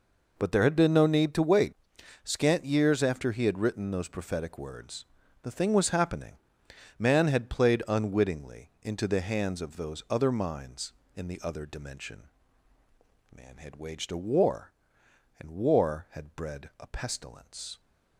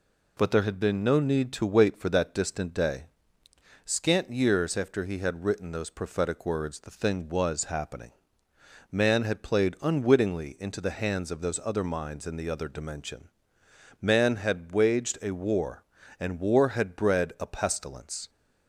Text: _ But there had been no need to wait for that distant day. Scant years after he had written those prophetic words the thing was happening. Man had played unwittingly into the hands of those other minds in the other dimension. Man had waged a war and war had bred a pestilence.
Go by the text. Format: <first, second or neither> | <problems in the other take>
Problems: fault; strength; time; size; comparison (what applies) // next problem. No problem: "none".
second | skips "for that distant day"; at 1.9 s // pauses between "words" and "the"; at 5.0 s; 0.38 s long